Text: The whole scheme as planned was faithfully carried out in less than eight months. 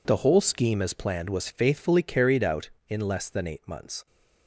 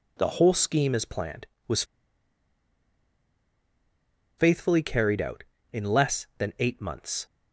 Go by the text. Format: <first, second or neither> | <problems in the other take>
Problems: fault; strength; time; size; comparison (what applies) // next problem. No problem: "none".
first | pauses between "was" and "faithfully"; strong; at 1.8 s; 2.5 s long